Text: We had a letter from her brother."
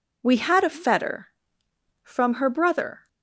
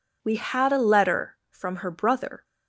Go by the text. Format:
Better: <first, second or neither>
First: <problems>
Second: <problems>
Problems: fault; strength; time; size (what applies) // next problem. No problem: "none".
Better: second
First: says "fetter" for "letter"; at 0.6 s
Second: none